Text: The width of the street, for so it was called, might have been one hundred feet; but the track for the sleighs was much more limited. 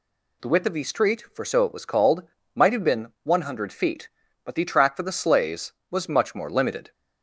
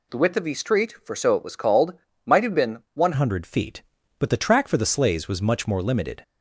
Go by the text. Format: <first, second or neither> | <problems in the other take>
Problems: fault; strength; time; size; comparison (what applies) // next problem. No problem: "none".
first | changes voice at "hundred"; from 3.1 s on; 3.1 s long